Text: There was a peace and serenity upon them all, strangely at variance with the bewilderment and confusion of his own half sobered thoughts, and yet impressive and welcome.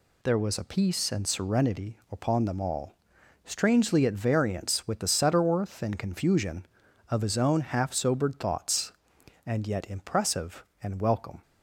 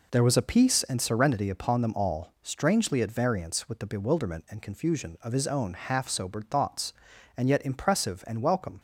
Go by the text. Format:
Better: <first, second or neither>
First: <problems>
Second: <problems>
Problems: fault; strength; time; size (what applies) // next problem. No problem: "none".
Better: second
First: says "setterworth" for "bewilderment"; at 5.0 s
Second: none